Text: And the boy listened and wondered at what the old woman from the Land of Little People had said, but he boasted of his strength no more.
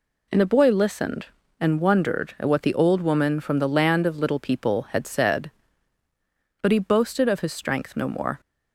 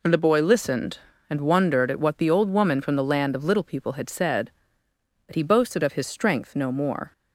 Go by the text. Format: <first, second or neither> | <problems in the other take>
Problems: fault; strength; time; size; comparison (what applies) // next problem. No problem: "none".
neither | none